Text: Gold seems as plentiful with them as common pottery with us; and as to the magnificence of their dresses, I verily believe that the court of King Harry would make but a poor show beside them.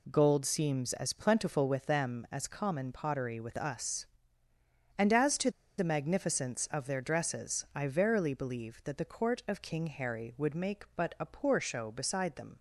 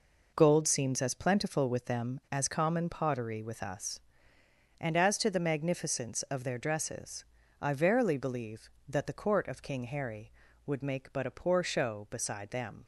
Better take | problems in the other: second | pauses between "to" and "the"; slight; at 5.5 s; 0.27 s long

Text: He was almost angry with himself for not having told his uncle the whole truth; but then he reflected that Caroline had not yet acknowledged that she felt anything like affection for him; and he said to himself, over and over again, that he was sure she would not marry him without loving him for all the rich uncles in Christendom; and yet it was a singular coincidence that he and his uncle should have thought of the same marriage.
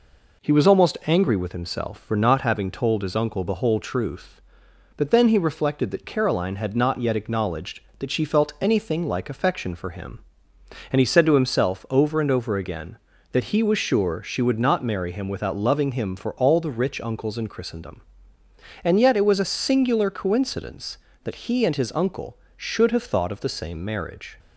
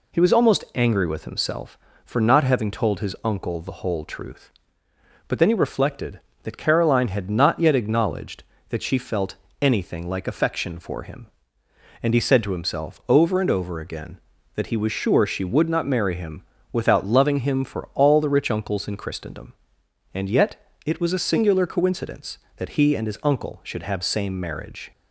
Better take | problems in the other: first | pauses between "felt" and "anything"; slight; at 9.3 s; 0.24 s long // pauses between "him" and "without"; slight; at 16.4 s; 0.30 s long // pauses between "yet" and "it"; slight; at 20.5 s; 0.28 s long // skips "thought of the"; at 24.0 s

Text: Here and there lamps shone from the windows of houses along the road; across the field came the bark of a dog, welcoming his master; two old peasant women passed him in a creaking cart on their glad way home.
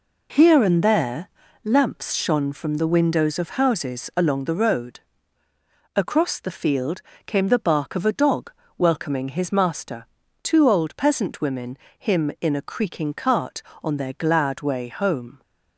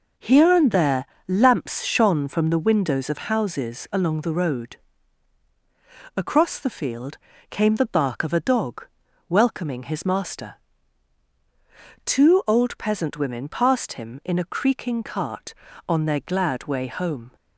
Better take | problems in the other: second | pauses between "there" and "lamps"; at 1.2 s; 0.38 s long; slight in the second // pauses between "field" and "came"; slight; at 7.0 s; 0.24 s long; slight in the second // skips "passed"; at 11.8 s

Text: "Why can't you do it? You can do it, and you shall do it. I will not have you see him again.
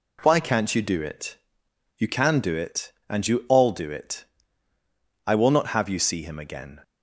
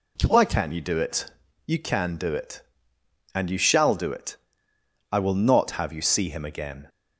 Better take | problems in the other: second | says "all" for "shall"; at 3.4 s

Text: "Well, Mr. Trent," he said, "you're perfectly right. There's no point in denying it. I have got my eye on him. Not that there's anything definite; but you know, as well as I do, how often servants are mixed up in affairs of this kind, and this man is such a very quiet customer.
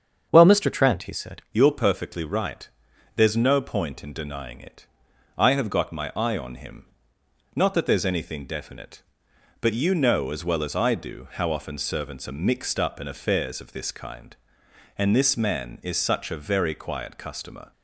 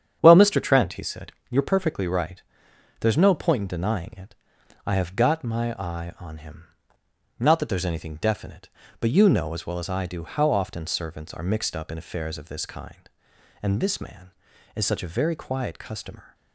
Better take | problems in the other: second | starts louder than the rest; strong; until 1.3 s; 7.5 dB; strong in the second // changes voice at "you're"; from 1.5 s on; 16.2 s long

